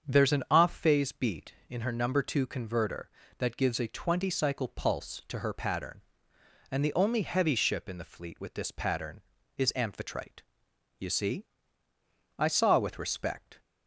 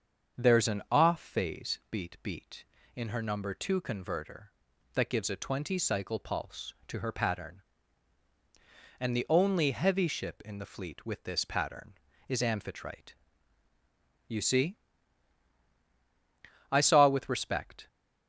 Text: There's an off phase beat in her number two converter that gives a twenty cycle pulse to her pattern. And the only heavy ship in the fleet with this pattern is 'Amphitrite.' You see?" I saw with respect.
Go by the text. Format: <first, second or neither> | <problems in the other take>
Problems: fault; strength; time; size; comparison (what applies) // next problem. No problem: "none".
first | starts louder than the rest; until 1.4 s; 7 dB; strong in the first // says "beat" twice; at 2.2 s